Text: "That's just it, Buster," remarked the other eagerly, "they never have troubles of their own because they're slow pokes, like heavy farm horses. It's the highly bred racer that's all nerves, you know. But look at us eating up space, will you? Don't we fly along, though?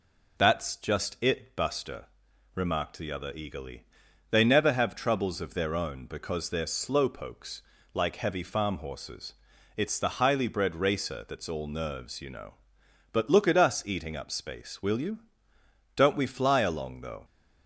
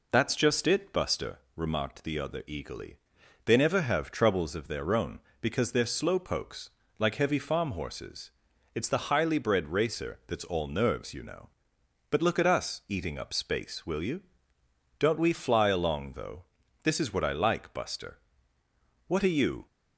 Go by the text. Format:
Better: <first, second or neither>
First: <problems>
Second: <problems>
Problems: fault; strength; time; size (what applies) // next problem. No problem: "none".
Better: first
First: none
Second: goes on to say "This is what I like Buster What are you"; strong; from 16.8 s on; 2.8 s long